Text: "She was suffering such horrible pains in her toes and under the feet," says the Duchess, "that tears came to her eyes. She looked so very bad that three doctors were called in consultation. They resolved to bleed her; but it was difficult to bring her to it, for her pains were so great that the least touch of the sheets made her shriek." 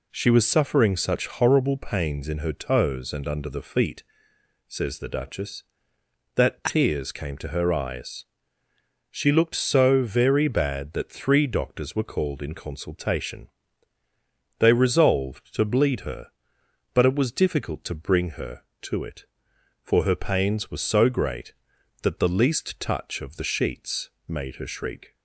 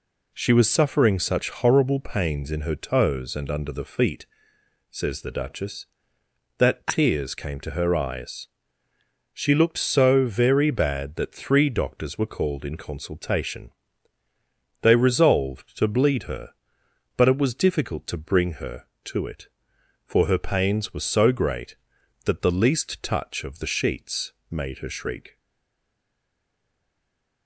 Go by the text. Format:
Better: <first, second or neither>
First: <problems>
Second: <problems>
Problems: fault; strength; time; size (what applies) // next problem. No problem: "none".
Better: first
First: pauses between "sheets" and "made"; slight; at 24.0 s; 0.18 s long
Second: pauses between "sheets" and "made"; slight; at 24.3 s; 0.18 s long // stays silent after the last word; from 25.3 s on; 2.1 s long